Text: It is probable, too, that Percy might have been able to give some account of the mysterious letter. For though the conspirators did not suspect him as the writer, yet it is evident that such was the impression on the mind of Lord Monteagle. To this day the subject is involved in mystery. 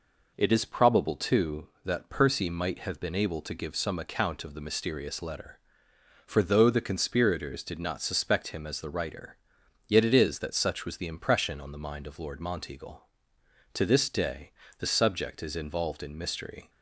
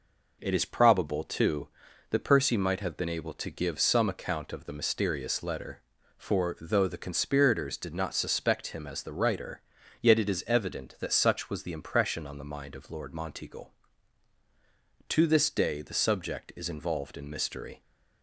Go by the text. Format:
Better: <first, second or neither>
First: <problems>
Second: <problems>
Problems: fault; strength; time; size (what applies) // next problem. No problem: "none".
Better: second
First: skips "evident"; at 10.3 s // pauses between "day" and "the"; slight; at 14.5 s; 0.28 s long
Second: none